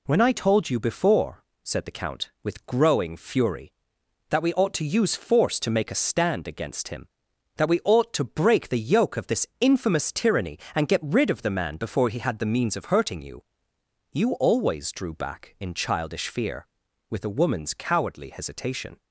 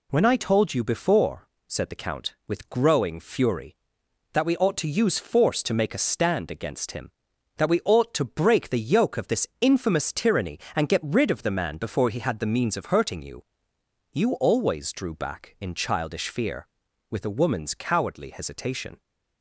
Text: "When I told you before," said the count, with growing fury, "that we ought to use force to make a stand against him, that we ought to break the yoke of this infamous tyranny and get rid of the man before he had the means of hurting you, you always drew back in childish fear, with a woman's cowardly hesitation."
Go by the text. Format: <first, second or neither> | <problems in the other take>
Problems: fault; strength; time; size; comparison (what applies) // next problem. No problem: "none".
neither | none